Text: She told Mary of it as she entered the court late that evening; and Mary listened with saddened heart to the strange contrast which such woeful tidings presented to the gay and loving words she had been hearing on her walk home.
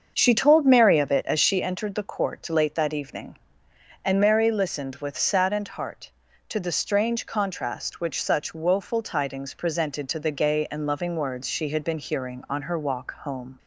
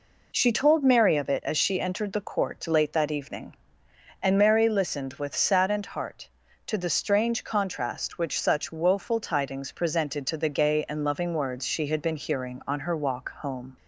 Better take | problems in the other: second | starts louder than the rest; until 1.7 s; 7 dB

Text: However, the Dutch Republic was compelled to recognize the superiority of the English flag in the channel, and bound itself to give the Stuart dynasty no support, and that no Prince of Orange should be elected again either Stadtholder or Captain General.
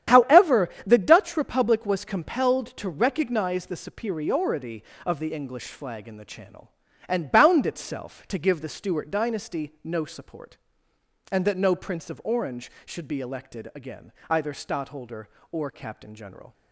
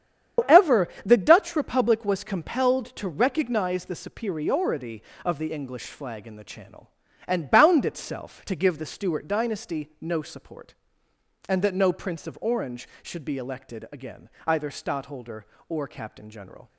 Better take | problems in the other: first | loses the start of "However"; at 0.3 s; 115 ms // starts louder than the rest; strong; until 1.5 s; 8.5 dB; strong in the first // pauses between "again" and "either"; slight; at 14.2 s; 0.20 s long; slight in the first

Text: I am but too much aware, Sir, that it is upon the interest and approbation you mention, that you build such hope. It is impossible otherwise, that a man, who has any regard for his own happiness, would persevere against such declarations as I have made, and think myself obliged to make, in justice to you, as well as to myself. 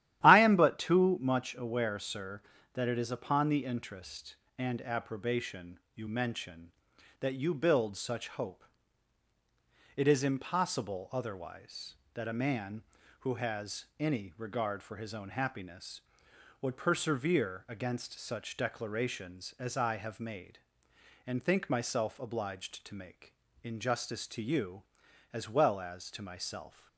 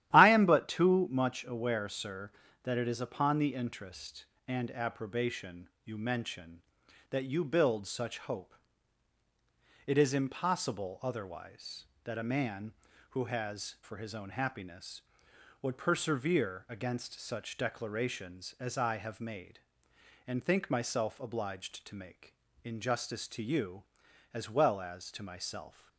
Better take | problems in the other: first | starts louder than the rest; strong; until 1.1 s; 12.5 dB; strong in the first // pauses between "approbation" and "you"; slight; at 5.6 s; 0.16 s long; slight in the first // skips "any regard"; at 13.7 s

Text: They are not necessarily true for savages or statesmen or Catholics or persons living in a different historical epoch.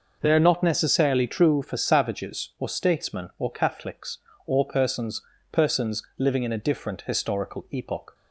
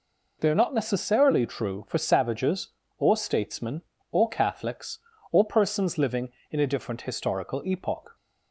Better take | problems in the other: second | says "persons" twice; at 5.5 s

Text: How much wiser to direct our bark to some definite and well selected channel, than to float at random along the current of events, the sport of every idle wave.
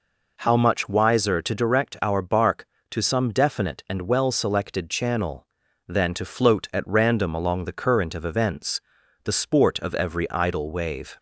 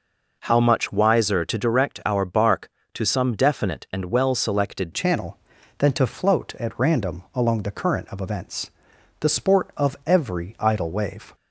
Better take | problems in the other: first | changes voice at "channel"; from 4.9 s on; 6.4 s long

